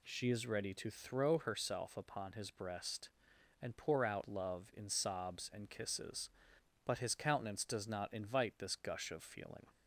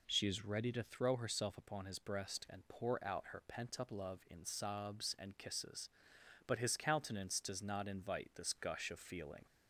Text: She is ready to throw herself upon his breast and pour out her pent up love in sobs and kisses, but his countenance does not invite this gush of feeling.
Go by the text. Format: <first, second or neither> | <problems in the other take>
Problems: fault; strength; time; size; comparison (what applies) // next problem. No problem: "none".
second | skips "her pent up"; at 4.2 s